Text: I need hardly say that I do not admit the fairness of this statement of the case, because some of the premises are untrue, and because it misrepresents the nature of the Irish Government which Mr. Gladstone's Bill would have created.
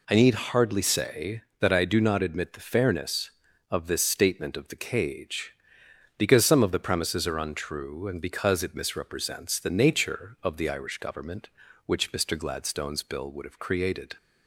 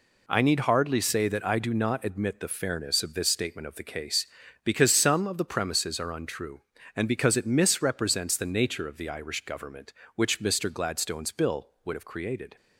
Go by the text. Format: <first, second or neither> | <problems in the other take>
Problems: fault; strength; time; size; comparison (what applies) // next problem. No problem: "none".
second | says "cage" for "case"; at 4.7 s